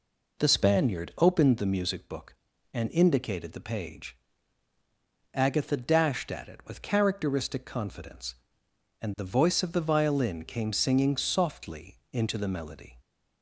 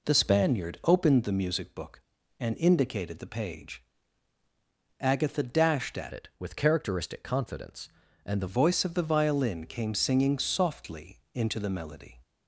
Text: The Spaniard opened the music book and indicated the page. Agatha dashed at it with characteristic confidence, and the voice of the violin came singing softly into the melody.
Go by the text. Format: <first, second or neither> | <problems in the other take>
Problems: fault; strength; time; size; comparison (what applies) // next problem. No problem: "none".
first | changes voice from "it" to "the"; from 6.1 to 8.4 s; 2.3 s long